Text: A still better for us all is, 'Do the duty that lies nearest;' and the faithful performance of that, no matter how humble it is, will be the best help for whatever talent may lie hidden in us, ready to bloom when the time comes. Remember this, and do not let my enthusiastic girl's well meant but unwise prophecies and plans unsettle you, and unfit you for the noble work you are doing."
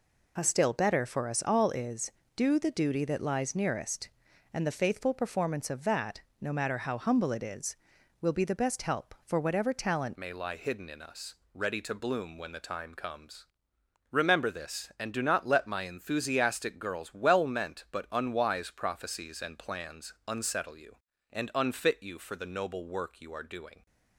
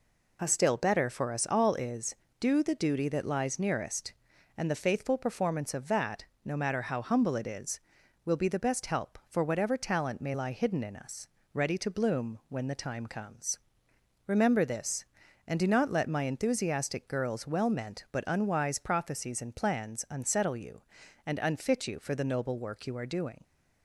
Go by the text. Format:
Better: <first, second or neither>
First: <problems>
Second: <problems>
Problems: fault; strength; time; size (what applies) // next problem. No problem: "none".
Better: second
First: changes voice at "may"; from 10.1 s on; 13.7 s long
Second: none